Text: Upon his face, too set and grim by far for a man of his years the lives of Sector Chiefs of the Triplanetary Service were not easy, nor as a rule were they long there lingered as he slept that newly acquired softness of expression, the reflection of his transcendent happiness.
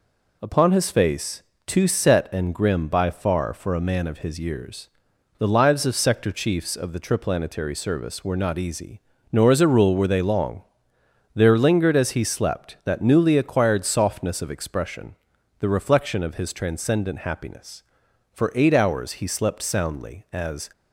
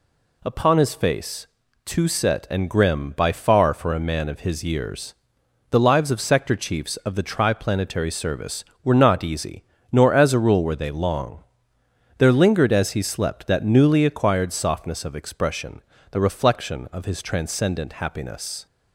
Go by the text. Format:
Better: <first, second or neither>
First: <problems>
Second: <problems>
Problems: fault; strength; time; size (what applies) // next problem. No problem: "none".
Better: second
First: pauses between "years" and "the"; noticeable; at 4.8 s; 0.50 s long // pauses between "long" and "there"; noticeable; at 10.6 s; 0.70 s long // goes on to say "For eight hours he slept soundly as"; strong; from 18.3 s on; 2.3 s long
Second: pauses between "years" and "the"; noticeable; at 5.1 s; 0.58 s long // pauses between "long" and "there"; noticeable; at 11.4 s; 0.76 s long